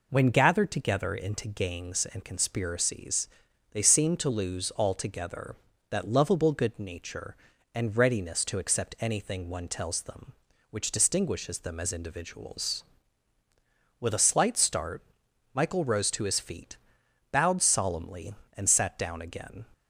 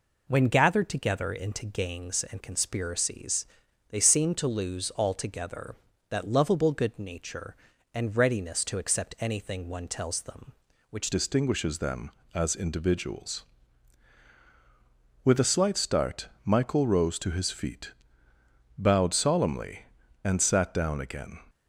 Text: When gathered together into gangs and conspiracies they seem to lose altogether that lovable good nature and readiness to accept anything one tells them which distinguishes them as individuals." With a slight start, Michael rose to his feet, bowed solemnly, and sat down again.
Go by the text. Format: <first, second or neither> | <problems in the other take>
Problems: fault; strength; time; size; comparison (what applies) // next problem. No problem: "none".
first | pauses between "conspiracies" and "they"; at 3.4 s; 0.42 s long; also in the first // changes voice at "distinguishes"; from 11.1 s on; 10.2 s long